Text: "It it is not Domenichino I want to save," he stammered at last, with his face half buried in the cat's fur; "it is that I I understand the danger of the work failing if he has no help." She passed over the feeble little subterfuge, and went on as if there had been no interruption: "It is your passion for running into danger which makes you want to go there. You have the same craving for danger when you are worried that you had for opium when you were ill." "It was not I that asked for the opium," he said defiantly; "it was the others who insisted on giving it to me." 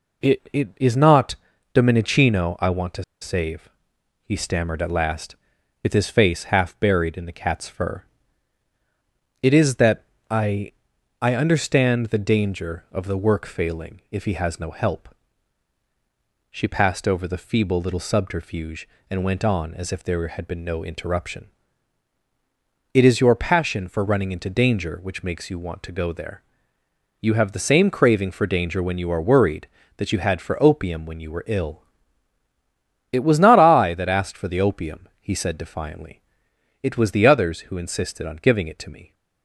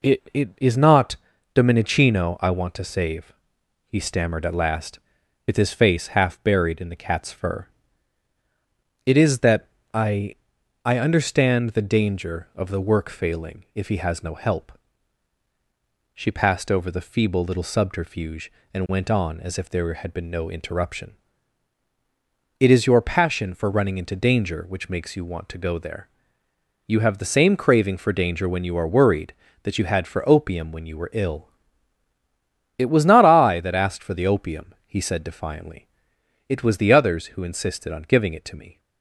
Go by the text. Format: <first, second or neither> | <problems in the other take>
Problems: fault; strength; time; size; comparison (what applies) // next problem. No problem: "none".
second | pauses between "not" and "Domenichino"; at 1.3 s; 0.40 s long; also in the second // pauses between "to" and "save"; slight; at 3.0 s; 0.19 s long // pauses between "that" and "I"; slight; at 10.0 s; 0.24 s long; slight in the second // pauses between "I" and "I"; noticeable; at 10.7 s; 0.50 s long; noticeable in the second